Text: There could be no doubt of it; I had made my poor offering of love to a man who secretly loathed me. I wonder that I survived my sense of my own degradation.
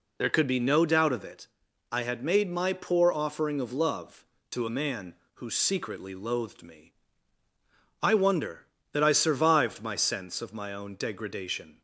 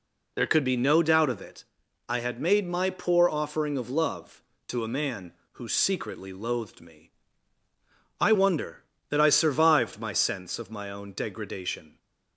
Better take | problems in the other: neither | none

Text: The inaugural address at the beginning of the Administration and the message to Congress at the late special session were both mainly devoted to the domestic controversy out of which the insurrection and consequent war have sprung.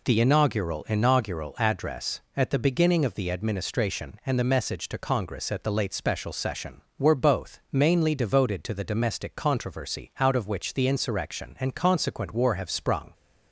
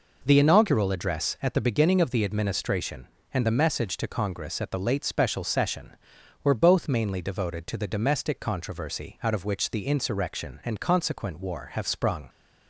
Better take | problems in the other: second | says "inaugural" twice; at 0.8 s

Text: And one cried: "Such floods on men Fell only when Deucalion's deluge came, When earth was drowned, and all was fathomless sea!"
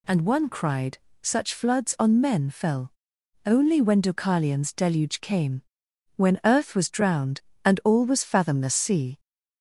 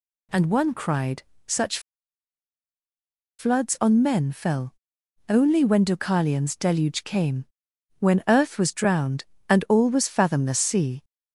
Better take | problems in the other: first | pauses between "Such" and "floods"; strong; at 1.7 s; 1.6 s long // pauses between "Fell" and "only"; noticeable; at 4.7 s; 0.56 s long; noticeable in the first

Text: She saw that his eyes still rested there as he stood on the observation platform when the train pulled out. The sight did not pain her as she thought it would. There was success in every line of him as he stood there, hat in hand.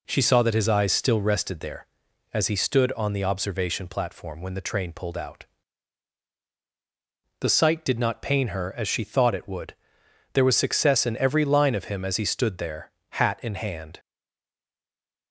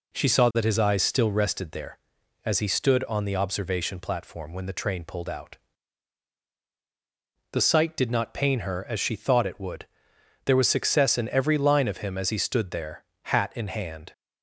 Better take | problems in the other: second | stays silent after the last word; noticeable; from 13.9 s on; 1.4 s long

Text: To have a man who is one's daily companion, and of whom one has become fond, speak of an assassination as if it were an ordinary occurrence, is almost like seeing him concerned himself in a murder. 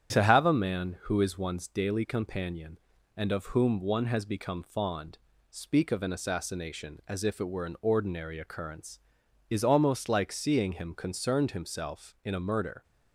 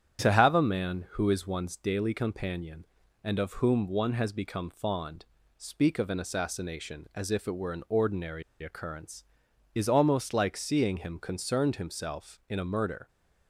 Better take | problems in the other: first | starts louder than the rest; strong; until 1.2 s; 9 dB; strong in the first // pauses between "ordinary" and "occurrence"; slight; at 8.4 s; 0.18 s long

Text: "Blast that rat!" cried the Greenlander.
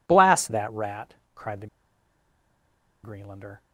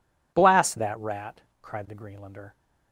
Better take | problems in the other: second | pauses between "the" and "Greenlander"; strong; at 1.6 s; 1.3 s long

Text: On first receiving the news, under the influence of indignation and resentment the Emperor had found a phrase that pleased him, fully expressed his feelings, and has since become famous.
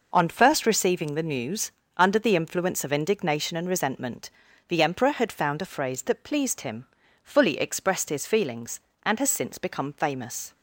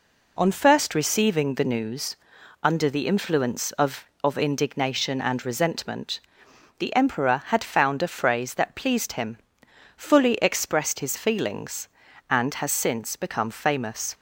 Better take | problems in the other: first | says "of" twice; at 4.2 s // pauses between "resentment" and "the"; noticeable; at 6.1 s; 0.60 s long; also in the first

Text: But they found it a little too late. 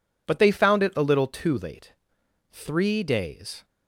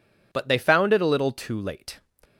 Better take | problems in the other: second | goes on to say "Three days"; noticeable; from 2.5 s on; 1.1 s long

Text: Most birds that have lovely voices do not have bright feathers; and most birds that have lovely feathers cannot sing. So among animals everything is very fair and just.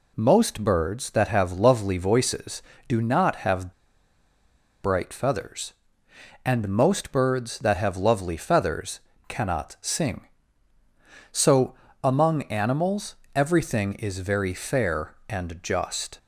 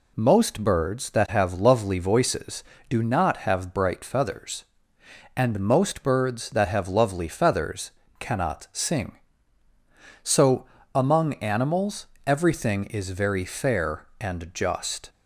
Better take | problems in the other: second | pauses between "have" and "bright"; at 3.7 s; 1.1 s long // pauses between "feathers" and "cannot"; slight; at 8.9 s; 0.30 s long; slight in the second // pauses between "So" and "among"; slight; at 11.7 s; 0.28 s long; slight in the second // pauses between "animals" and "everything"; slight; at 13.1 s; 0.18 s long; slight in the second

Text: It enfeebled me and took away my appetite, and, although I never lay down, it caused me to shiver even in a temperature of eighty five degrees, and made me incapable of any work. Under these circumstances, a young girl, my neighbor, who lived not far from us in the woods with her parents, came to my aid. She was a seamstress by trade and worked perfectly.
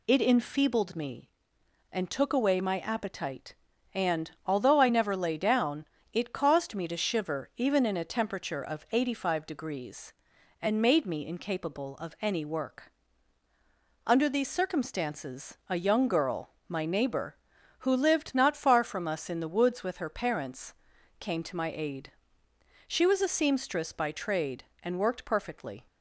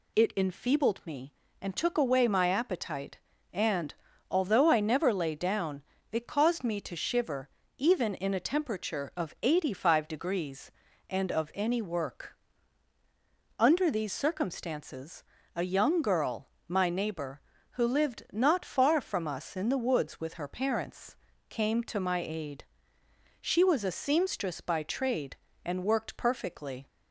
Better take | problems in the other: first | pauses between "shiver" and "even"; slight; at 7.4 s; 0.30 s long // skips "made me incapable"; at 11.3 s

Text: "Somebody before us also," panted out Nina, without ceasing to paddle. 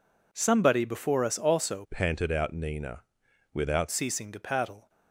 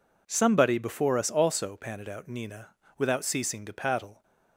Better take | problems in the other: second | changes voice from "panted" to "without"; from 1.9 to 3.8 s; 1.9 s long

